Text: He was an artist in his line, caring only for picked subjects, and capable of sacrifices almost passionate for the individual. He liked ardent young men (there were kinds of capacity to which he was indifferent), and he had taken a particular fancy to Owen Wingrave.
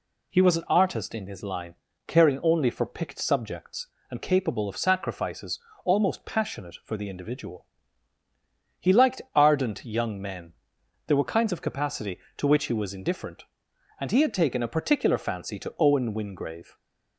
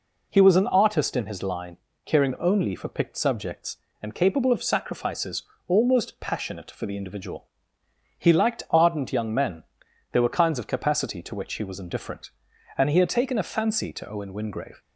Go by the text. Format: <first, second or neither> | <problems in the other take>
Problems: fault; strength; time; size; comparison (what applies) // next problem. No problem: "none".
first | pauses between "sacrifices" and "almost"; slight; at 5.4 s; 0.24 s long; slight in the first // skips "particular"; at 13.4 s